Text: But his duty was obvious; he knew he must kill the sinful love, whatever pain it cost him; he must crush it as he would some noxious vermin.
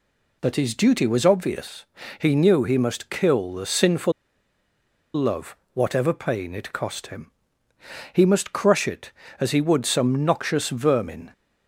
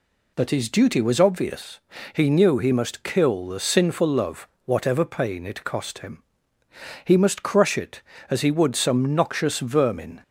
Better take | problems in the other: second | pauses between "sinful" and "love"; at 4.1 s; 1.0 s long

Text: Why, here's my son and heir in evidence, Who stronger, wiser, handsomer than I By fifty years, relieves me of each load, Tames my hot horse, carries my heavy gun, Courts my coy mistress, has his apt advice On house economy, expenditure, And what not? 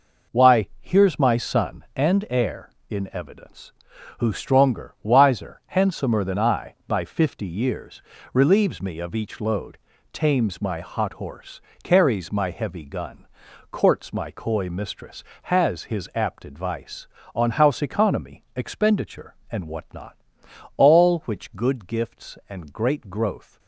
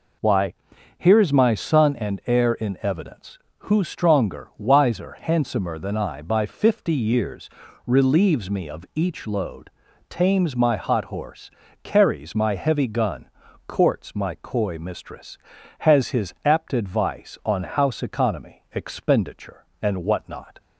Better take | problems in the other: second | goes on to say "All which good gifts and great growth"; strong; from 20.7 s on; 2.8 s long

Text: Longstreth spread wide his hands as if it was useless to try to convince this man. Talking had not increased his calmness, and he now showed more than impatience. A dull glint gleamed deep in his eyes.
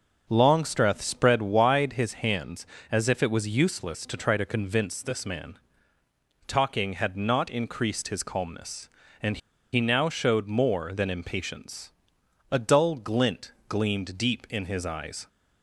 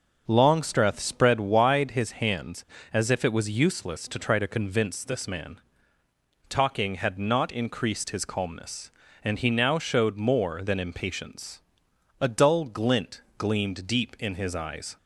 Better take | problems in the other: second | starts louder than the rest; noticeable; until 1.3 s; 6 dB; noticeable in the second // pauses between "and" and "he"; slight; at 9.3 s; 0.35 s long // pauses between "glint" and "gleamed"; slight; at 13.5 s; 0.16 s long; slight in the second

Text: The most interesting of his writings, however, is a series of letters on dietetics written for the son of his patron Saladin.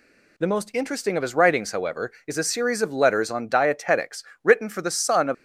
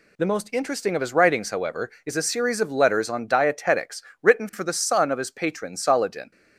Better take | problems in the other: second | pauses between "dietetics" and "written"; slight; at 4.2 s; 0.20 s long; slight in the second // stops before "his patron Saladin"; at 5.3 s

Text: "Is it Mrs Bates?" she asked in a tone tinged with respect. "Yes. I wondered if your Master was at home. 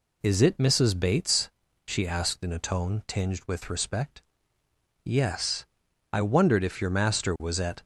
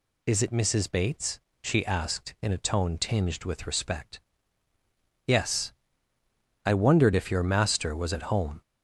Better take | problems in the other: second | stops before "home"; at 7.8 s

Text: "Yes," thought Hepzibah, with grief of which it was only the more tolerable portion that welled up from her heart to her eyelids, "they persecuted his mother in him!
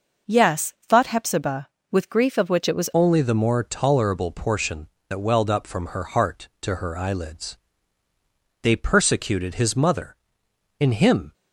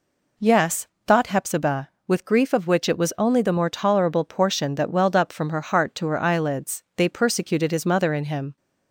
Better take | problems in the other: second | changes voice at "only"; from 2.9 s on; 8.4 s long

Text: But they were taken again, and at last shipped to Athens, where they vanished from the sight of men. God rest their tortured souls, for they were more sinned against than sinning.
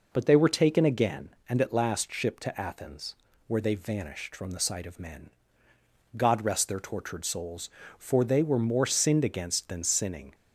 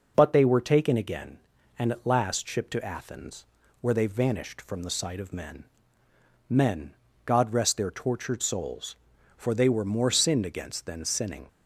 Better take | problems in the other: first | says "men" twice; at 6.4 s

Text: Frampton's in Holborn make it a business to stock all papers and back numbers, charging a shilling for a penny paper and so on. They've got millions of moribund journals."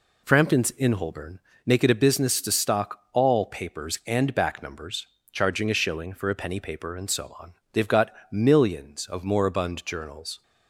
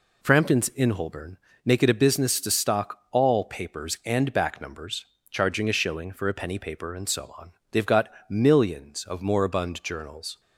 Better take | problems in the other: neither | pauses between "Holborn" and "make"; slight; the same in both // pauses between "got" and "millions"; slight; the same in both

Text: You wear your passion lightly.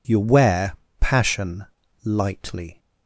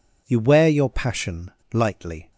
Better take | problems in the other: second | skips "your"; at 0.8 s // pauses between "passion" and "lightly"; at 1.6 s; 0.39 s long; slight in the second

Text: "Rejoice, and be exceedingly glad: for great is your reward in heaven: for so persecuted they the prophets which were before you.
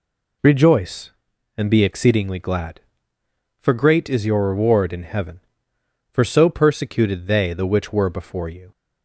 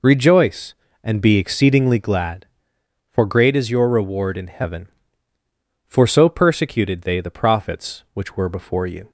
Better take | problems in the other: second | skips "prophets"; at 7.6 s

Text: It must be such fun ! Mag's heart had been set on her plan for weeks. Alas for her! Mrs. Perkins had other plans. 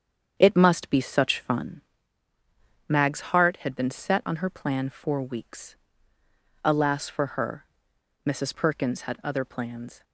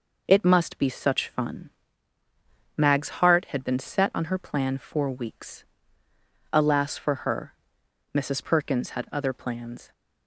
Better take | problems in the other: second | starts louder than the rest; strong; until 1.7 s; 8 dB

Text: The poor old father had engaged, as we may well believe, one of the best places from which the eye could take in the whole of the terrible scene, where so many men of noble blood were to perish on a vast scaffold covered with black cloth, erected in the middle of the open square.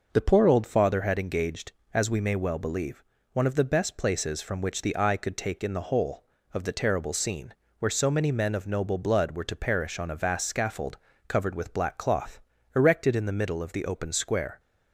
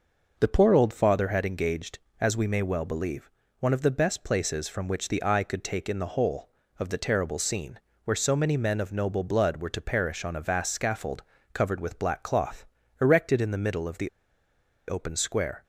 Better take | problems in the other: first | pauses between "scaffold" and "covered"; slight; at 11.2 s; 0.32 s long; slight in the first // pauses between "the" and "open"; noticeable; at 14.0 s; 0.79 s long

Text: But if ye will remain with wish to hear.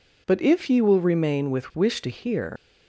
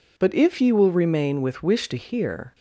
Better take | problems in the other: second | leaves "hear" unfinished; at 2.5 s; 115 ms

